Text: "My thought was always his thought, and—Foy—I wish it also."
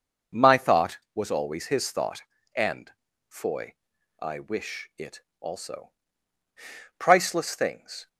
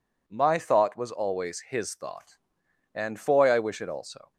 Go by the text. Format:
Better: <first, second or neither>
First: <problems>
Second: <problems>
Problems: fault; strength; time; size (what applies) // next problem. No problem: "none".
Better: second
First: pauses between "it" and "also"; slight; at 5.2 s; 0.18 s long // goes on to say "Priceless things"; noticeable; from 6.9 s on; 1.1 s long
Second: none